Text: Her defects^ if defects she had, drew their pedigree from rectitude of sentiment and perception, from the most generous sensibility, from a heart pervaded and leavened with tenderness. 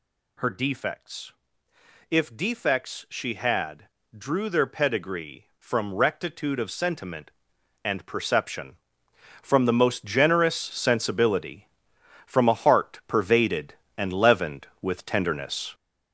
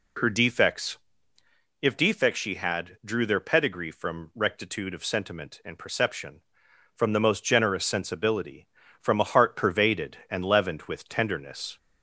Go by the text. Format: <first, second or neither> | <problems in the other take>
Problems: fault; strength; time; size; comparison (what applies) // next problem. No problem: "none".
second | gets louder; throughout; 6.5 dB // pauses between "defects" and "if"; noticeable; at 1.3 s; 0.80 s long; noticeable in the second